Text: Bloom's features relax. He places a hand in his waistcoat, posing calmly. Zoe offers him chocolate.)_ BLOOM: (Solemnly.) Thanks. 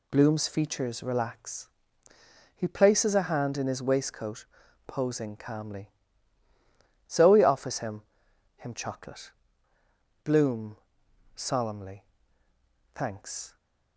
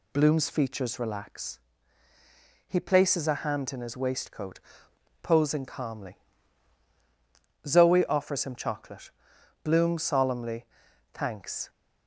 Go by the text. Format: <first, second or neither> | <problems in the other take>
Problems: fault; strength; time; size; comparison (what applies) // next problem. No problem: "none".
second | says "him" twice; at 8.5 s